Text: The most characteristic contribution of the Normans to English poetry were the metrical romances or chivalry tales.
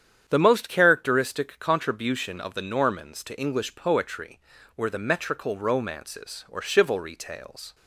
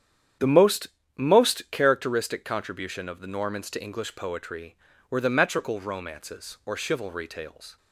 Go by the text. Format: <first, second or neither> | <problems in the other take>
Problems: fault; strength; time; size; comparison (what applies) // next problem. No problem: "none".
first | starts louder than the rest; strong; until 1.6 s; 9 dB; strong in the first // says "most" twice; at 1.1 s